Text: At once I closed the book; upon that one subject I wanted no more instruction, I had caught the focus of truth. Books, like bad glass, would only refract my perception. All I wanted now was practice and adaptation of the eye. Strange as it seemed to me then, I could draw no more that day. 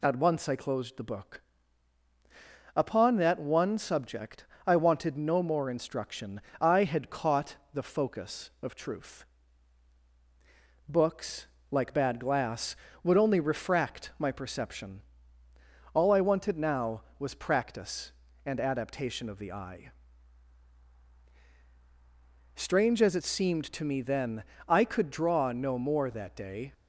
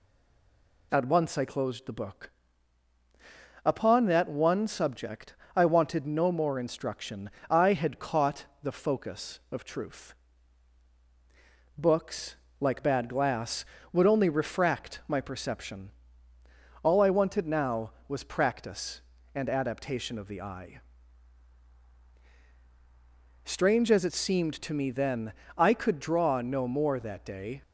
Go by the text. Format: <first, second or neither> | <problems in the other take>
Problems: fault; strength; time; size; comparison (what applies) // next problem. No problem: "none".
first | stays silent before the first word; slight; until 0.9 s; 0.9 s long // pauses between "subject" and "I"; slight; at 5.3 s; 0.18 s long; slight in the first // pauses between "caught" and "the"; slight; at 8.4 s; 0.18 s long; slight in the first